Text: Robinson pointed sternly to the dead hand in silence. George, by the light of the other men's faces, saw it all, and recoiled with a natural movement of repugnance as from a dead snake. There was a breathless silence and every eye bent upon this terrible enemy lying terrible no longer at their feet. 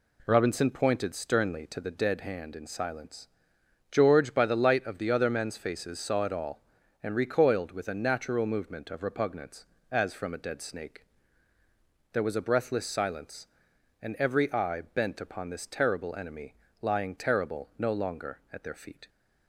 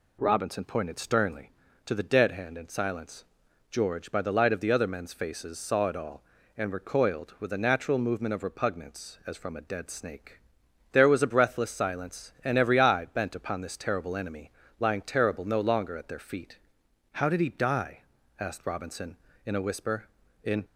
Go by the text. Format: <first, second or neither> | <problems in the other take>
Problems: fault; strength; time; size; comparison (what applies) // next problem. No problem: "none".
first | pauses between "enemy" and "lying"; slight; at 14.5 s; 0.28 s long; slight in the first // goes on to say "How did he die asked Robinson in a whisper In"; strong; from 17.1 s on; 3.5 s long